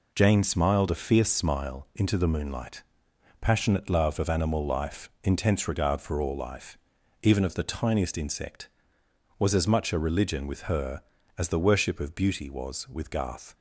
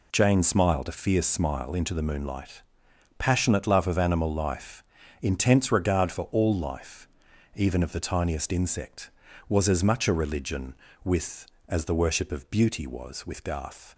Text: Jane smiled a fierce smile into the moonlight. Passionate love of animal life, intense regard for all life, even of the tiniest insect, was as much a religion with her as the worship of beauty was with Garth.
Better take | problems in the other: first | skips "her"; at 11.5 s

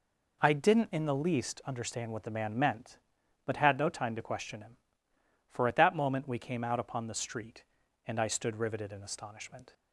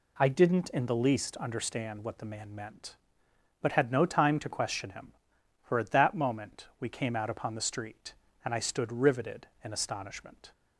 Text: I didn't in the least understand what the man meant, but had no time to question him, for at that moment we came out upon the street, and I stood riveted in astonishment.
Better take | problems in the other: neither | none

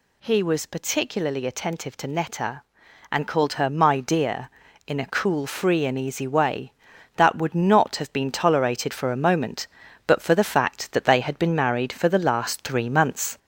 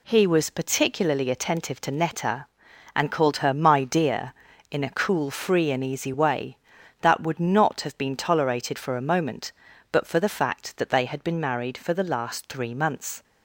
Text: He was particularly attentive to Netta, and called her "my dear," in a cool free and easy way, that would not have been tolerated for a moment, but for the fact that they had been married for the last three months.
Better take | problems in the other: second | gets louder; slight; throughout; 2.5 dB

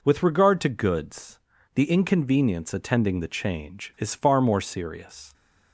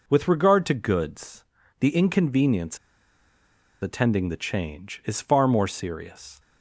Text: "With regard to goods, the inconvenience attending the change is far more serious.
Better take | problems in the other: first | pauses between "inconvenience" and "attending"; at 2.7 s; 1.0 s long

